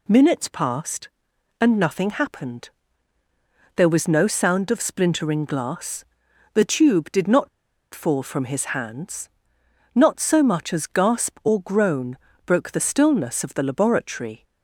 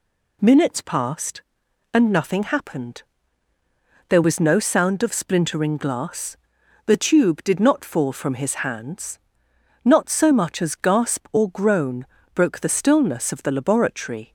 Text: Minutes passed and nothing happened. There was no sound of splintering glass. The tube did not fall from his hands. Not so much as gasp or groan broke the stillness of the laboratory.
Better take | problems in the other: second | pauses between "not" and "fall"; at 7.4 s; 0.44 s long // pauses between "groan" and "broke"; slight; at 12.1 s; 0.30 s long; slight in the second

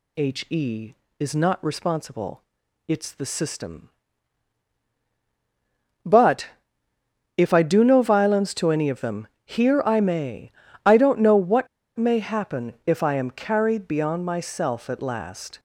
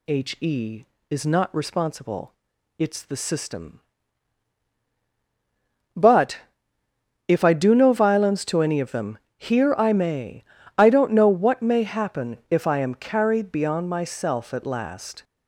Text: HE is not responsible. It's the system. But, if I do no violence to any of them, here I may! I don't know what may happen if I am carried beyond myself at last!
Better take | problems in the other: second | pauses between "what" and "may"; slight; at 11.6 s; 0.30 s long

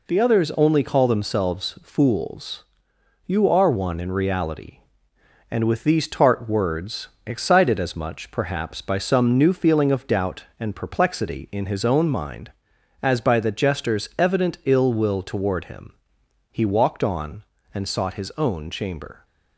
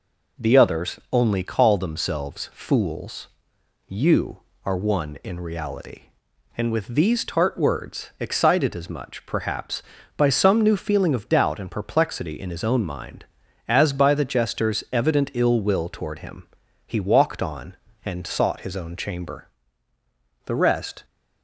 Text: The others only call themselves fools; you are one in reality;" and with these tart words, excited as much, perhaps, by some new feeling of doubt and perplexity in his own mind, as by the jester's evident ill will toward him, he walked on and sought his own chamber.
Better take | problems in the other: first | goes on to say "The rest"; from 20.4 s on; 0.60 s long

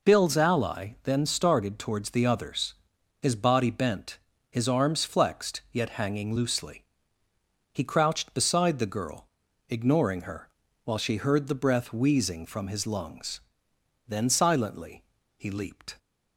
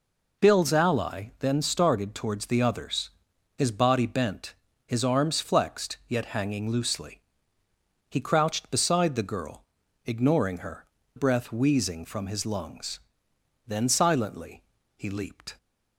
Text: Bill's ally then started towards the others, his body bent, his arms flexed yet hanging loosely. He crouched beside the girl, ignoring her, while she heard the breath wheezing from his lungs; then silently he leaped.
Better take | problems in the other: first | skips "while she heard the"; at 11.0 s // pauses between "silently" and "he"; slight; at 14.6 s; 0.34 s long; slight in the first

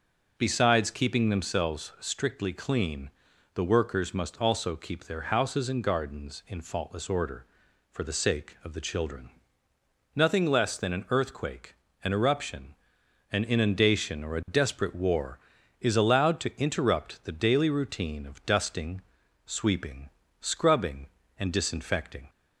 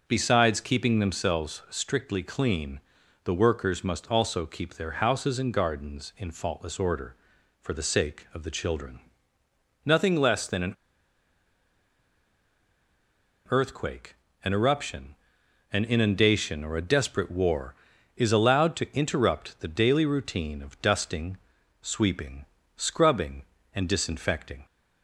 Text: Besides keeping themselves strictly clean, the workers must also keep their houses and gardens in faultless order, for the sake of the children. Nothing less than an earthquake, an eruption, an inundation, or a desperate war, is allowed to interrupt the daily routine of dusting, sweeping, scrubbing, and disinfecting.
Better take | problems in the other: first | pauses between "an" and "earthquake"; strong; at 10.7 s; 2.7 s long

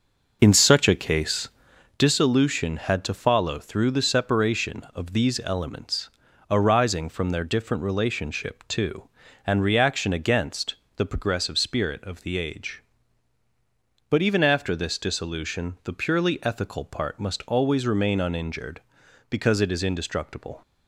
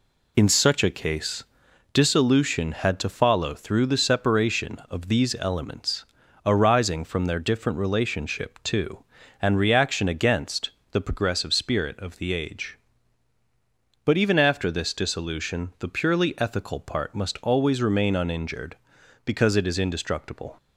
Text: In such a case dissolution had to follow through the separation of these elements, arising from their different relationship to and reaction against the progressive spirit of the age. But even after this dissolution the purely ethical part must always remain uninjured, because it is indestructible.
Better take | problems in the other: second | starts louder than the rest; noticeable; until 2.0 s; 5.5 dB // pauses between "case" and "dissolution"; noticeable; at 1.4 s; 0.48 s long; noticeable in the second // pauses between "against" and "the"; slight; at 10.7 s; 0.20 s long; slight in the second

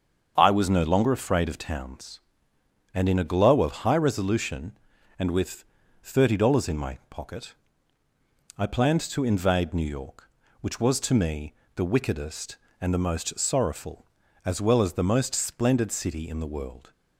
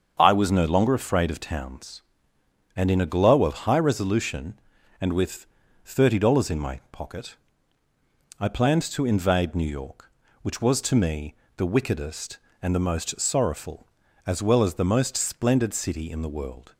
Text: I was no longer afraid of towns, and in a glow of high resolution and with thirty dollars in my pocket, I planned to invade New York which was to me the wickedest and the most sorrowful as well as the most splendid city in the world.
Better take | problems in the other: neither | starts louder than the rest; the same in both // pauses between "with" and "thirty"; the same in both // pauses between "me" and "the"; slight; the same in both

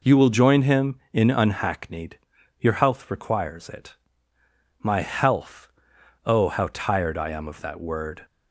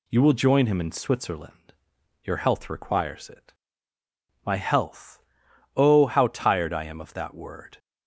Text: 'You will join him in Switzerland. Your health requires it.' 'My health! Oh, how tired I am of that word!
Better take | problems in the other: second | says "Unhackneyed" for "Switzerland"; at 1.3 s

